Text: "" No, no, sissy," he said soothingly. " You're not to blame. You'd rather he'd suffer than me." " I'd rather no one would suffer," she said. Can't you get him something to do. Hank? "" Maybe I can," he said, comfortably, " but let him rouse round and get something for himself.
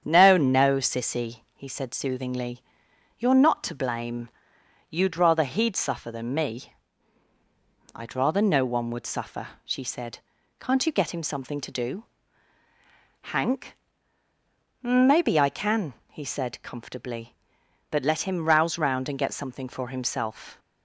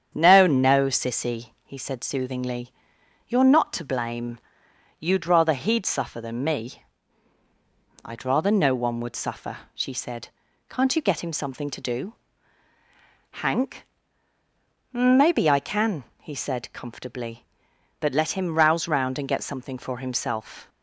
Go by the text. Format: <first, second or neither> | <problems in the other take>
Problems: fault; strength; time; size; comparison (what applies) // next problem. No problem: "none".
neither | starts louder than the rest; strong; the same in both